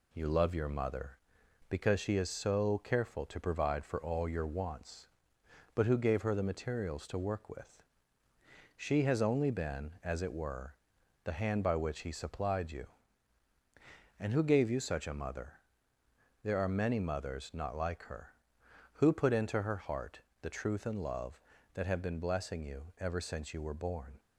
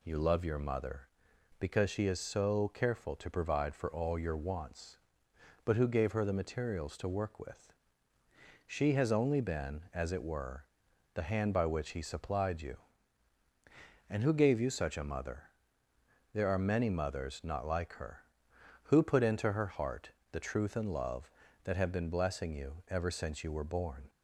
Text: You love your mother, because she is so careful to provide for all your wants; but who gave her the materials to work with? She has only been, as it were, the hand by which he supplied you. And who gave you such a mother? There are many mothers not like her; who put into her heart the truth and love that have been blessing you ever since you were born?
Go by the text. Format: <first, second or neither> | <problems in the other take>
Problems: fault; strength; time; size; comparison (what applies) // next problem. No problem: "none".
second | gets quieter; slight; throughout; 3.5 dB // pauses between "heart" and "the"; slight; at 20.2 s; 0.18 s long; slight in the second